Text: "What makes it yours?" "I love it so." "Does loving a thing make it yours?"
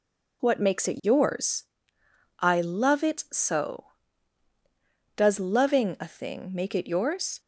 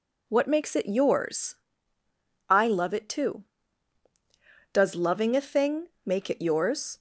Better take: first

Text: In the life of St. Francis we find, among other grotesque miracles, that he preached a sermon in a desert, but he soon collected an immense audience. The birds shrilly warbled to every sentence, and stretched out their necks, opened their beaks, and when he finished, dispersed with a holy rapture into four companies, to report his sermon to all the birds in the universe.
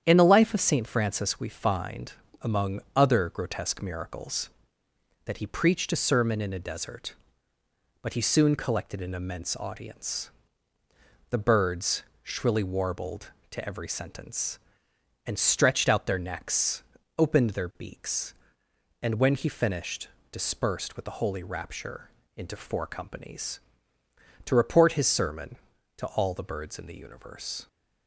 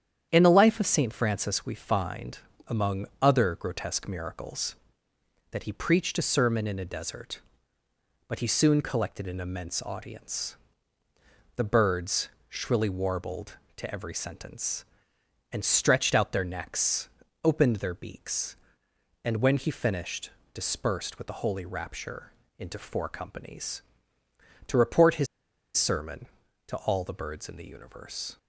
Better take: first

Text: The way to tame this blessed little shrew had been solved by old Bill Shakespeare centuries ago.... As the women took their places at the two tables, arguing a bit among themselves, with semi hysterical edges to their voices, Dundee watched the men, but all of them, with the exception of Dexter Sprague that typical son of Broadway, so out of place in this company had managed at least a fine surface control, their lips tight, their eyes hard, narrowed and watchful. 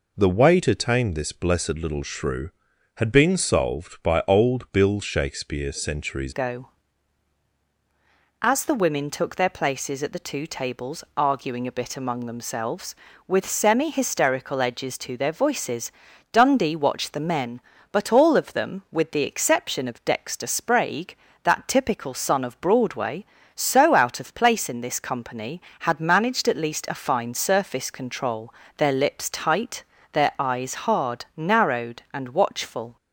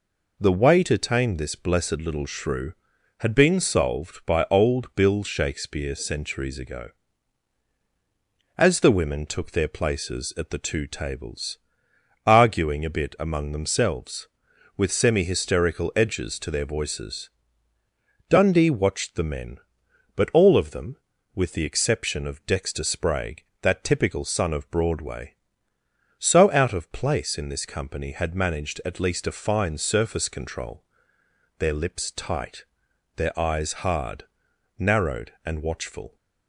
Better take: second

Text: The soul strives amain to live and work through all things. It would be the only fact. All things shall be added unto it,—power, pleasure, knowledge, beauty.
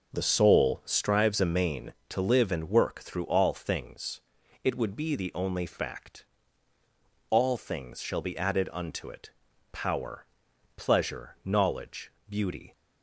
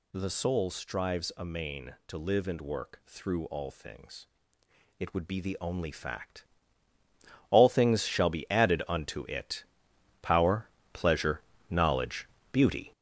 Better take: first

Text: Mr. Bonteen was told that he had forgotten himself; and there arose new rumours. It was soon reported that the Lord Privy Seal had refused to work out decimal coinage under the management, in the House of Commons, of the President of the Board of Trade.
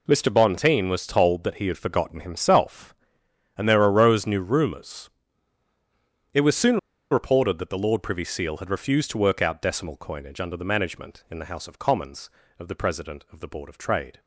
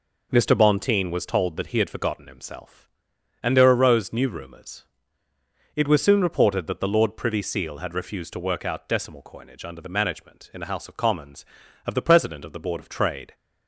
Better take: second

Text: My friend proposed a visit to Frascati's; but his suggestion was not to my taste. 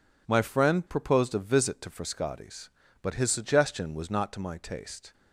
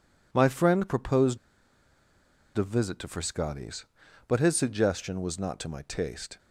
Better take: first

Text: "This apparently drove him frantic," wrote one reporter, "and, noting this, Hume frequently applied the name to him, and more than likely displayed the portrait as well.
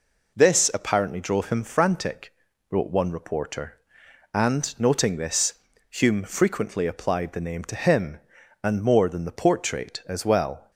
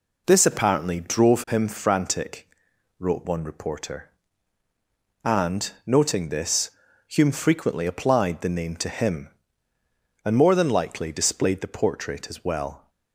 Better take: second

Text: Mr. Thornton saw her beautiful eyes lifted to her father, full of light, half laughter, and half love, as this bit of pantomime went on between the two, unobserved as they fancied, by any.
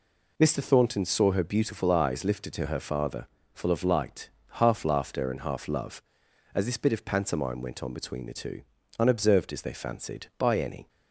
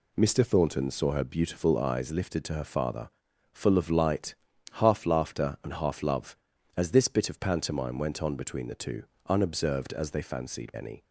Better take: first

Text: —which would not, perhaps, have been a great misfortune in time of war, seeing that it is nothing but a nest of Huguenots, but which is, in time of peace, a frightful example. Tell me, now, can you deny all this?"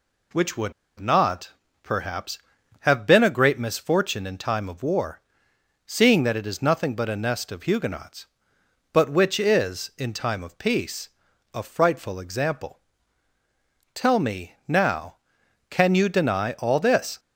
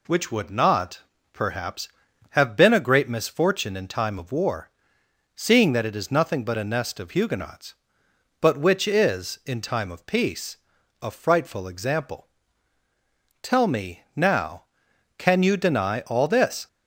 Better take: second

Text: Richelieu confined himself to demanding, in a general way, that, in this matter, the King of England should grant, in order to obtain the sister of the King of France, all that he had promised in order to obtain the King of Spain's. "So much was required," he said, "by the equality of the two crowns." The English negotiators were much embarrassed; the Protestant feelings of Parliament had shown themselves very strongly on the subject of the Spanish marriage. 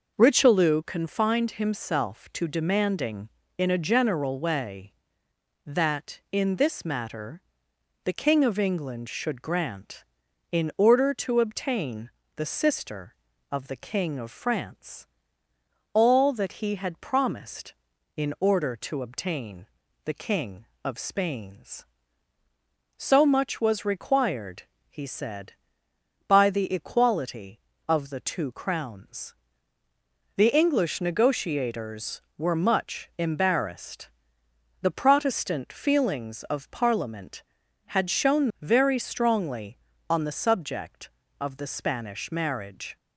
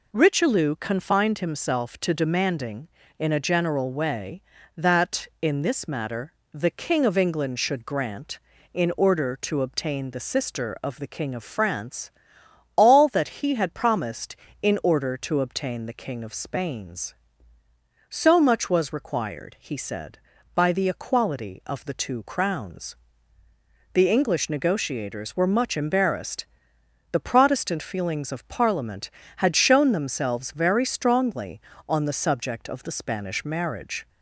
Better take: second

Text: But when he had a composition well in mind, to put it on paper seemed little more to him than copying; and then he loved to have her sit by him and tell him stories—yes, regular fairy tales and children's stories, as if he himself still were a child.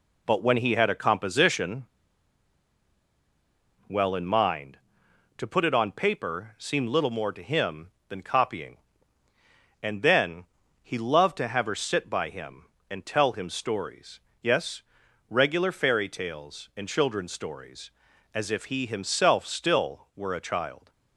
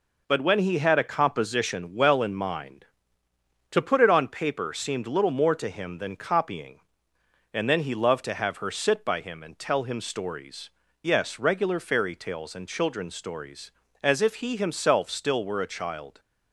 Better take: second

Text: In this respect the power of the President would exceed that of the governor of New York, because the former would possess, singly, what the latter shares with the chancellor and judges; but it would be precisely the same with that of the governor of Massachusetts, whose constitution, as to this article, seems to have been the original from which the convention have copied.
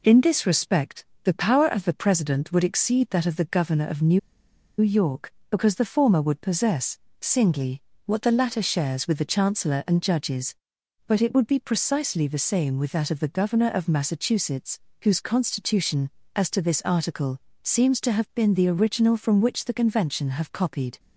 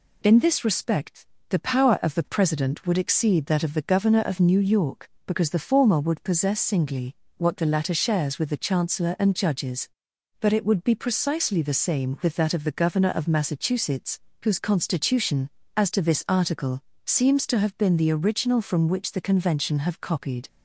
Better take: second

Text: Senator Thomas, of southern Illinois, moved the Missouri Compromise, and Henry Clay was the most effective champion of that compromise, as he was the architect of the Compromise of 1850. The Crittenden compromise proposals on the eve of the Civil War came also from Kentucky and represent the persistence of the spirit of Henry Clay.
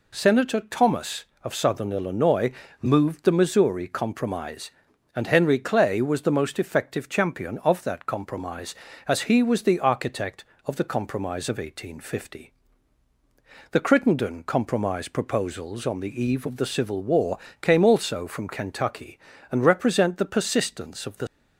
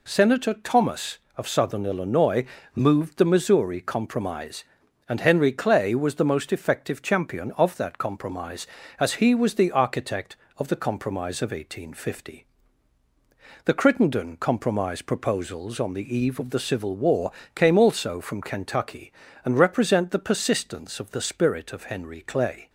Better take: second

